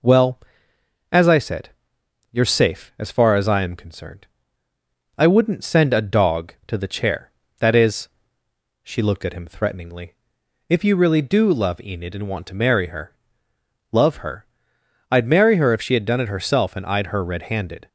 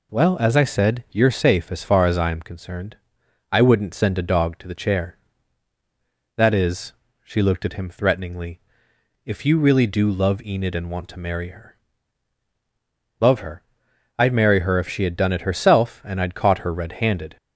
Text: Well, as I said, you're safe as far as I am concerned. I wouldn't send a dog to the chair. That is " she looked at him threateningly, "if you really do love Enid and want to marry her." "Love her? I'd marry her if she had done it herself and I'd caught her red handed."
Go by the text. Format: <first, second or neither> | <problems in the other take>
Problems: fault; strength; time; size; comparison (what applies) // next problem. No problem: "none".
second | skips "caught"; at 17.0 s